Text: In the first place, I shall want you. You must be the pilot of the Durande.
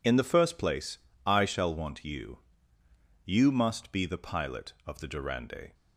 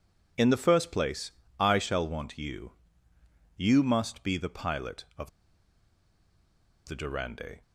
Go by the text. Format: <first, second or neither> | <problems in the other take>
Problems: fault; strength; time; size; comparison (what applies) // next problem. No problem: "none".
first | pauses between "of" and "the"; strong; at 5.2 s; 1.5 s long